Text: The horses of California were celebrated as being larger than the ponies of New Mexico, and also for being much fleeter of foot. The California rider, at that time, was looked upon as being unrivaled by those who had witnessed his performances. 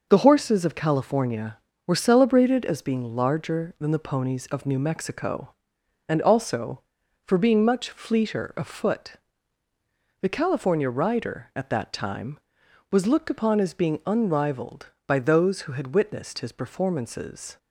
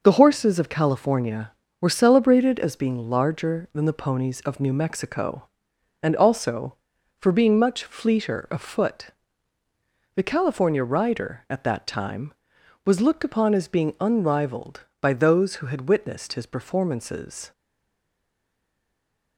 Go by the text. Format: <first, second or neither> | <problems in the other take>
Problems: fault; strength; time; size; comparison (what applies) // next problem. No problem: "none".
first | stays silent after the last word; noticeable; from 17.5 s on; 1.8 s long